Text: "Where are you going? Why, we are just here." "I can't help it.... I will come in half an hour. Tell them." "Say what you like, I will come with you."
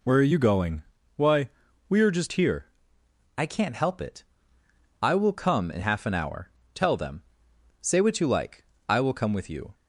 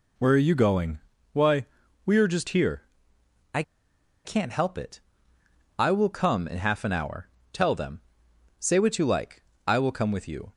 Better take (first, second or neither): first